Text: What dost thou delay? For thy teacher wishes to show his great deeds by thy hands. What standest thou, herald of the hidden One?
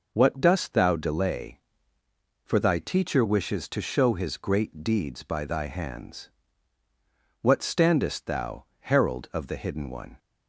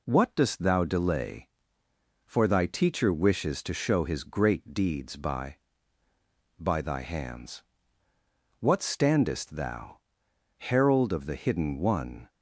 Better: first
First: none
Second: says "by" twice; at 6.5 s

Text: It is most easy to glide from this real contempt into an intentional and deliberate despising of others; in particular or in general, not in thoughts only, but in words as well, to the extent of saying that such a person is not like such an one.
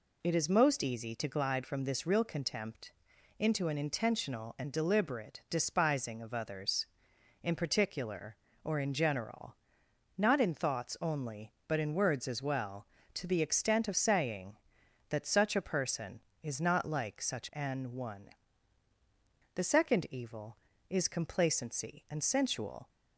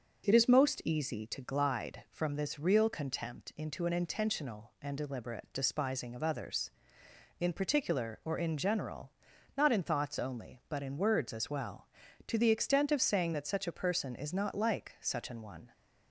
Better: second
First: pauses between "contempt" and "into"; noticeable; at 2.9 s; 0.46 s long // goes on to say "The second evil is complacency and sensual"; strong; from 19.5 s on; 3.3 s long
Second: none

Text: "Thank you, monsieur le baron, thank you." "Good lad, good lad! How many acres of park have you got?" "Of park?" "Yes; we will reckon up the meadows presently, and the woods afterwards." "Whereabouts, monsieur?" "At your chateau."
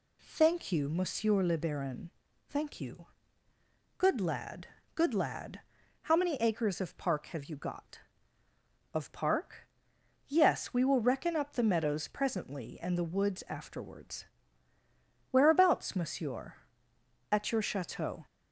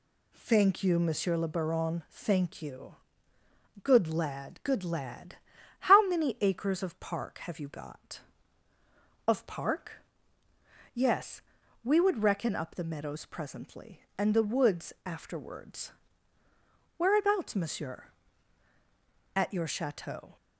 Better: first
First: none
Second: says "would" for "will"; at 11.9 s

